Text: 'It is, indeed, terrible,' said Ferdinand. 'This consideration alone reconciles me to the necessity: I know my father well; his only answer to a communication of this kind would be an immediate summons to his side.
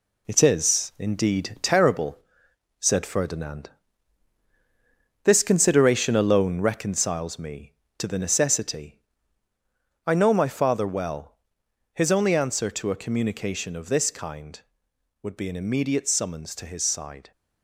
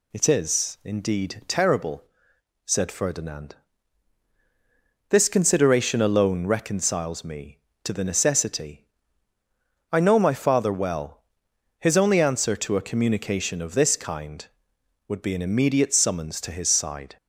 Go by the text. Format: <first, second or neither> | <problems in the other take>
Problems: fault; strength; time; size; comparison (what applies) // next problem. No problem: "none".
second | gets quieter; noticeable; throughout; 6 dB